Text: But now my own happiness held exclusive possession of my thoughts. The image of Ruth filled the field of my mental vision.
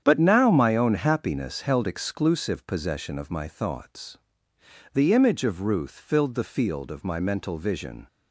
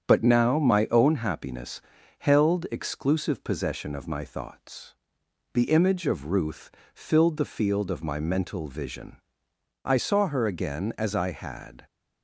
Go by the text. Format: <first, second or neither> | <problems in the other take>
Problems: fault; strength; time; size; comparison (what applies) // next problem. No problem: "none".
first | starts louder than the rest; strong; until 1.1 s; 7.5 dB; strong in the first // pauses between "happiness" and "held"; at 1.7 s; 0.40 s long // pauses between "Ruth" and "filled"; slight; at 6.6 s; 0.24 s long // goes on to say "I saw her again as I had"; strong; from 9.8 s on; 2.0 s long